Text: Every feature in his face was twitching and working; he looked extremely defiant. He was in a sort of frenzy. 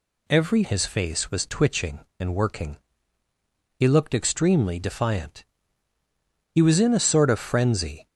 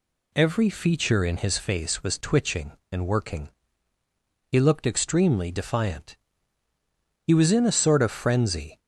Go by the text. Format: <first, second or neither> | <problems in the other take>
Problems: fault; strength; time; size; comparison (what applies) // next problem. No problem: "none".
second | skips "feature in"; at 0.6 s